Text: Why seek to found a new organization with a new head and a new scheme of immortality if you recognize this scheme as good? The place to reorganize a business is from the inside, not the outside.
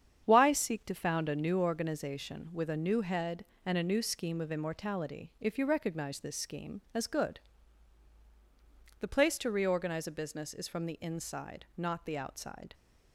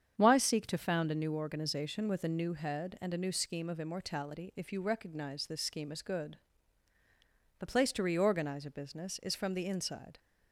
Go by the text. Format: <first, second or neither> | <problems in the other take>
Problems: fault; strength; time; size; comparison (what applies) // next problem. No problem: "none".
first | starts louder than the rest; strong; until 1.2 s; 8 dB; strong in the first // stops before "not the outside"; at 10.1 s